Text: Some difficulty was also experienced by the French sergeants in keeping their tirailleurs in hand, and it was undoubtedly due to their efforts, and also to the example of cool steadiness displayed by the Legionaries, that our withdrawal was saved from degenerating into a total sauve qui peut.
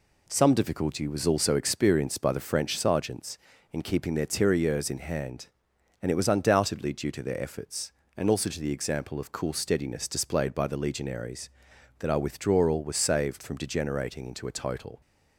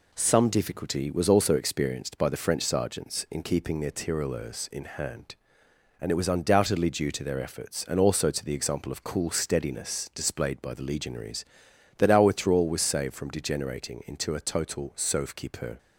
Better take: second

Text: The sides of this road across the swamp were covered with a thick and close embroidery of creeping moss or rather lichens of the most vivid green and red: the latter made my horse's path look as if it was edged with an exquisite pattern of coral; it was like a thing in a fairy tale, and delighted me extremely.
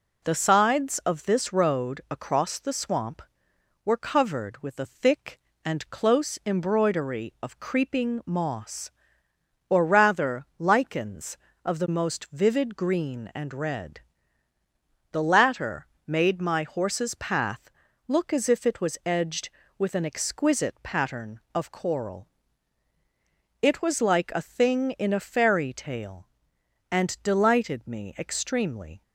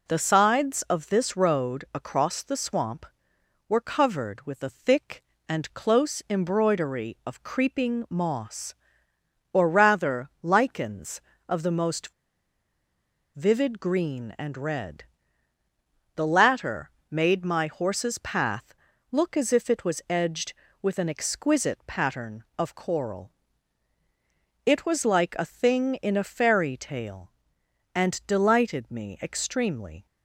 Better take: first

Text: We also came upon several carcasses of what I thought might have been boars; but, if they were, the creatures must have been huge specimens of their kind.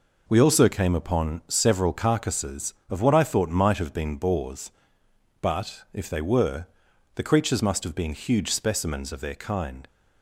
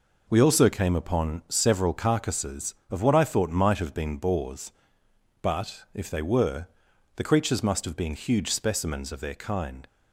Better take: neither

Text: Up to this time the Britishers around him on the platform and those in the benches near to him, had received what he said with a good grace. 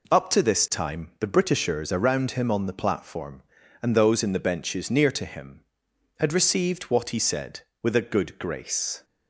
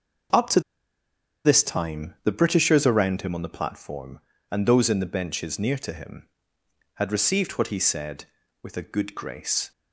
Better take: first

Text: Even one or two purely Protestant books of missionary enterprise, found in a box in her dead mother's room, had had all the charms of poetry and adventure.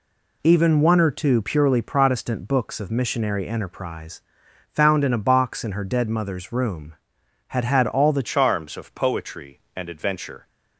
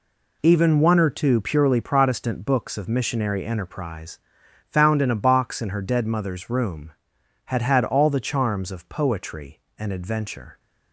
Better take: second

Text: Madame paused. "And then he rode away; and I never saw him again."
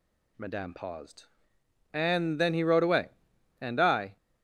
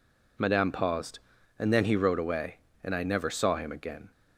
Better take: second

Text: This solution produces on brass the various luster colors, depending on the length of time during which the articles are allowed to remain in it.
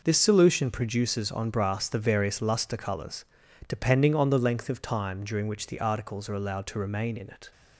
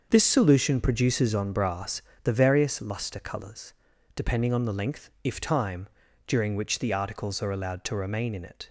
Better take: first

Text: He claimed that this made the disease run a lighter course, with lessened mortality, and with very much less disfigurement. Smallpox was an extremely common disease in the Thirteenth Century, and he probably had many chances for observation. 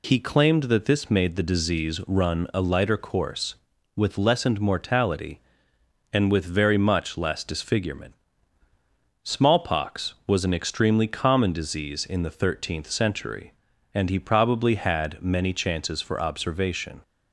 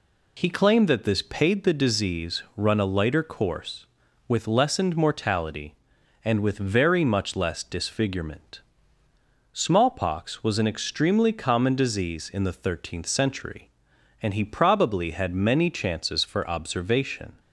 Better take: first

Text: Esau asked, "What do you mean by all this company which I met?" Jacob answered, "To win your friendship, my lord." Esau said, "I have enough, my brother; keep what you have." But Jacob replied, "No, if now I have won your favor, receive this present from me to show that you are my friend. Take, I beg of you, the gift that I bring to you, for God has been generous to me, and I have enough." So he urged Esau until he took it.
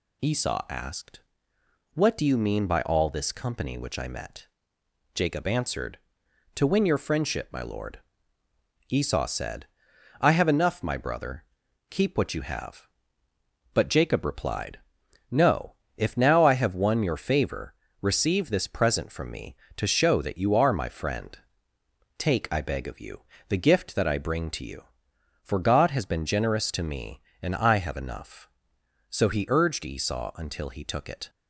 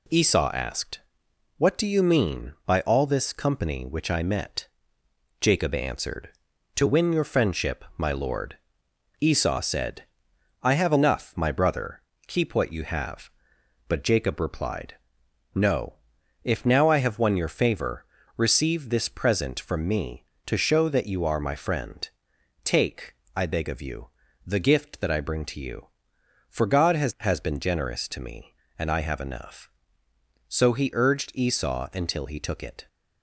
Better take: first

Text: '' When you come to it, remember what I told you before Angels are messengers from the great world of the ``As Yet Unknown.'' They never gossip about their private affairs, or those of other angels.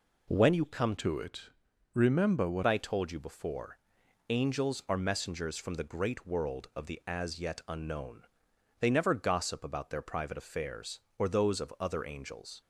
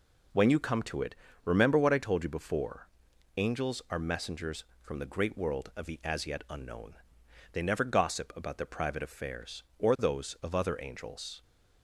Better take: second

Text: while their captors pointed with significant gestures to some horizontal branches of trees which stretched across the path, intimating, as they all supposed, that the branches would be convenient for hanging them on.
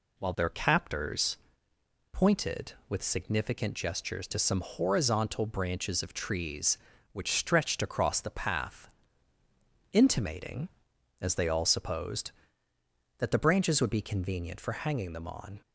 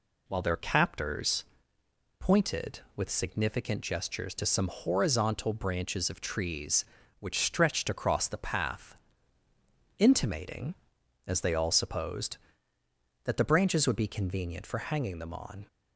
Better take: neither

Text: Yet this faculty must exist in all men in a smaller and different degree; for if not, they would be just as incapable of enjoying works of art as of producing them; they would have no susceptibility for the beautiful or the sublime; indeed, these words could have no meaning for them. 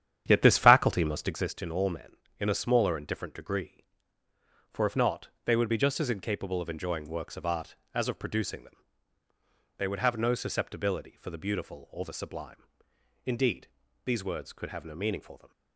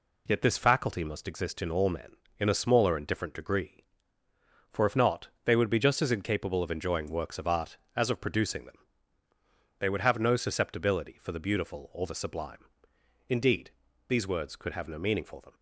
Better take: second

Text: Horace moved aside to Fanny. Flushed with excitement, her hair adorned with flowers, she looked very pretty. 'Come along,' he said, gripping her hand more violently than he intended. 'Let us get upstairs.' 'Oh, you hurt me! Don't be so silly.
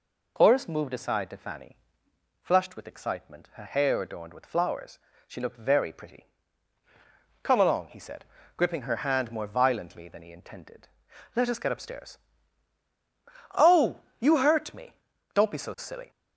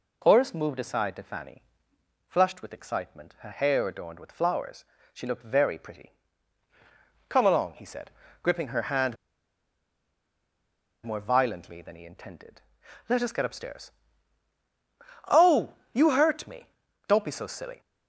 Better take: first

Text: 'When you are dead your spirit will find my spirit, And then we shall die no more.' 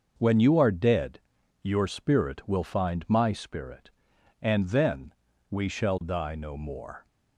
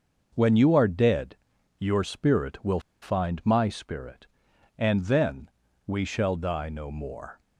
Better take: first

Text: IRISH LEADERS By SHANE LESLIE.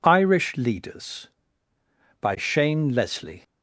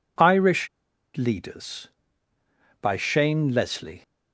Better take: first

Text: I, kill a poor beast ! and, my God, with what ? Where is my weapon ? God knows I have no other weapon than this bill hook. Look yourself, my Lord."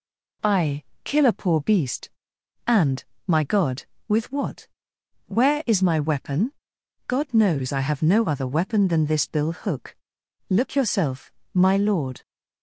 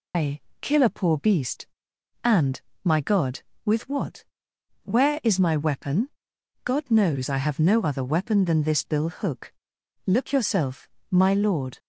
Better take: first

